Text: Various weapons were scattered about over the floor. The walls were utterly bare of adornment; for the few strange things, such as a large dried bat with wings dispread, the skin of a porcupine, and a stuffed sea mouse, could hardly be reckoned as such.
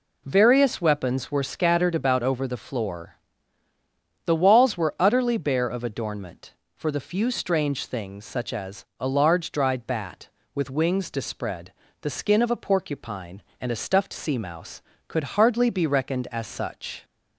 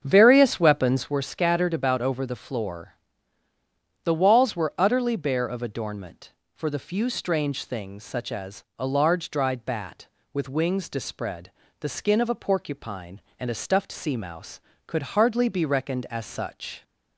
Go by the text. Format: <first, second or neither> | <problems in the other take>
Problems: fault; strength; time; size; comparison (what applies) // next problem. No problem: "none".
first | starts louder than the rest; strong; until 1.2 s; 7 dB